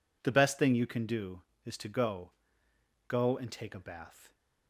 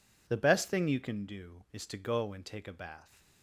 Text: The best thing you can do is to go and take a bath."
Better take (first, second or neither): second